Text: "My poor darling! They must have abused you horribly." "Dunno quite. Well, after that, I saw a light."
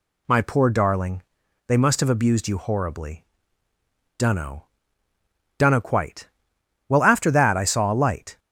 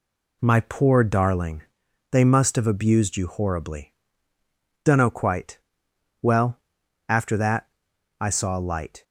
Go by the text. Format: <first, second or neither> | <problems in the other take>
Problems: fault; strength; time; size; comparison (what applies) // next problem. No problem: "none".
second | says "Dunno" twice; at 5.5 s